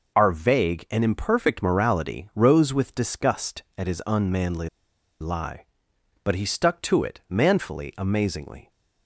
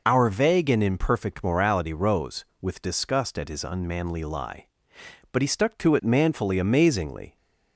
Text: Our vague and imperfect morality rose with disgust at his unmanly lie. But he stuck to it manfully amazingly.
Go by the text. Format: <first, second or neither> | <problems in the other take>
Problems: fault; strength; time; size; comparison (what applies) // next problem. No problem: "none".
second | pauses between "unmanly" and "lie"; noticeable; at 4.6 s; 0.52 s long